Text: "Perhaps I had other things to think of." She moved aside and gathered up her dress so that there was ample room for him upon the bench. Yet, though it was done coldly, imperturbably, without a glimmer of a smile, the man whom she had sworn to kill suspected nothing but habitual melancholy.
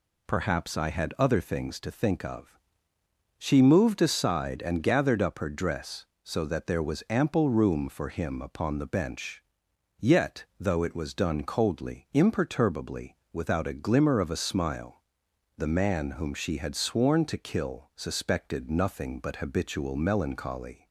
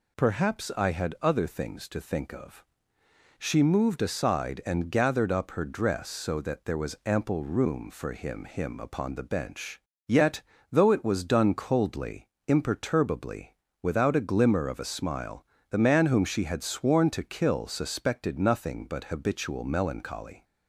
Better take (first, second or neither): first